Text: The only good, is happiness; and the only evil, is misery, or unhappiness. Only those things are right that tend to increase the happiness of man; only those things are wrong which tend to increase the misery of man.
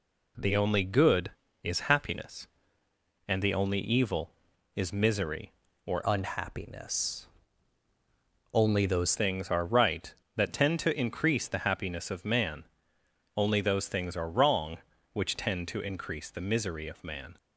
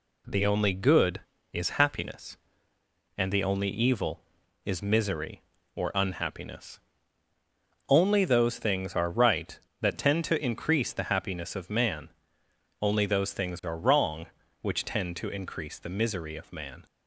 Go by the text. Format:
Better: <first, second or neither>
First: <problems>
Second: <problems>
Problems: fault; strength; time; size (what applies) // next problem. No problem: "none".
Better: second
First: changes voice from "unhappiness" to "those"; from 6.0 to 9.1 s; 3.1 s long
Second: none